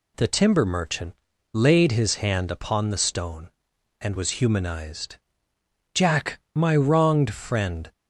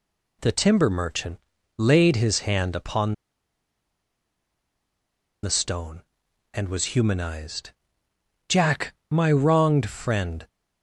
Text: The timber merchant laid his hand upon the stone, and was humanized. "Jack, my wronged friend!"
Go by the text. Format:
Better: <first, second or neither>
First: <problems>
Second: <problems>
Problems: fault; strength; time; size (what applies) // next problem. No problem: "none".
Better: first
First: pauses between "merchant" and "laid"; at 1.1 s; 0.40 s long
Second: pauses between "merchant" and "laid"; at 1.3 s; 0.40 s long // pauses between "upon" and "the"; strong; at 3.1 s; 2.2 s long